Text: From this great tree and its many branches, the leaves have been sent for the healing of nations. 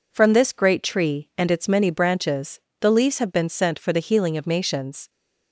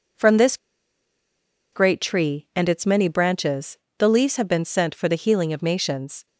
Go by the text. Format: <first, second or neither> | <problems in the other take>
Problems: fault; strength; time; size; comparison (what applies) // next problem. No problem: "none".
first | pauses between "this" and "great"; at 0.5 s; 1.1 s long